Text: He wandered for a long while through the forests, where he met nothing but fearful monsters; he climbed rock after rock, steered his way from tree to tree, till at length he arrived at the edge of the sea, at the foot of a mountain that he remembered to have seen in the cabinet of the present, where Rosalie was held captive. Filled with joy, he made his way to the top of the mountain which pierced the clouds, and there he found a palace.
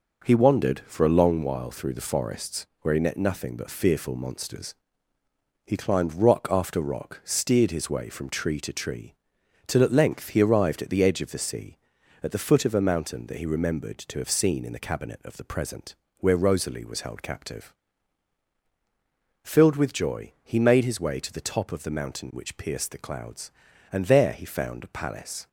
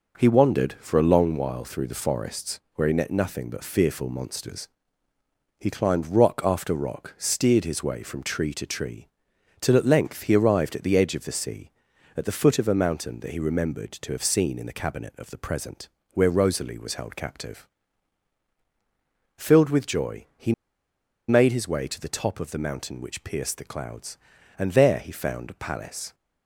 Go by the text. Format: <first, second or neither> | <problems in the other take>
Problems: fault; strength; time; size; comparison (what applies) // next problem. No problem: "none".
first | pauses between "he" and "made"; noticeable; at 20.5 s; 0.76 s long